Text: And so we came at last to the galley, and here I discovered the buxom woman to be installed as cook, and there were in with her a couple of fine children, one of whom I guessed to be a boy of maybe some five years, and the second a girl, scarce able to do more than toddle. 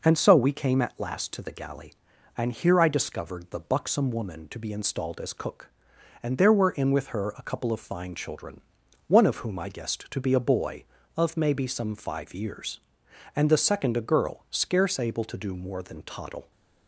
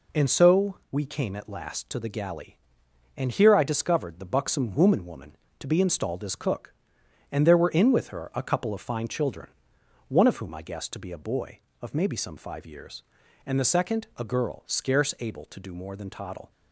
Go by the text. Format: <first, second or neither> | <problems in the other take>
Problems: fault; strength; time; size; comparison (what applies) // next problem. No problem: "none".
first | says "woman" twice; at 5.0 s